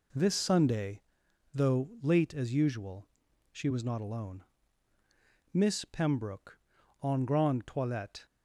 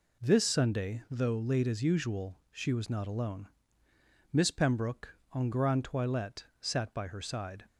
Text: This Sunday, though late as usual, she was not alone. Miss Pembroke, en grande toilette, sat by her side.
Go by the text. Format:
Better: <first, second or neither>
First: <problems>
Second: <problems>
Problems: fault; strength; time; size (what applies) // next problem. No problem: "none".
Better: second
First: stops before "sat by her side"; at 8.2 s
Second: none